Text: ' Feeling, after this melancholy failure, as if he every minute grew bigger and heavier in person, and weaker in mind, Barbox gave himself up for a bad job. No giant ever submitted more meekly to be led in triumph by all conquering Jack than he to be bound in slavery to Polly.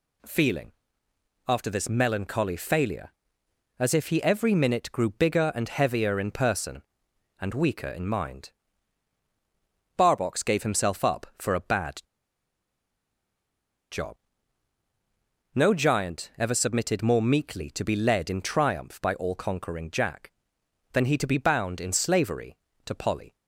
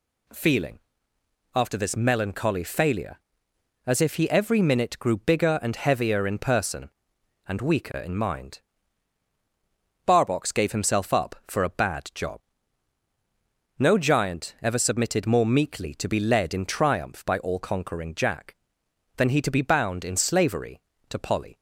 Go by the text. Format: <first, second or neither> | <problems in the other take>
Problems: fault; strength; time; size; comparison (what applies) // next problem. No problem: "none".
second | pauses between "bad" and "job"; strong; at 12.0 s; 1.8 s long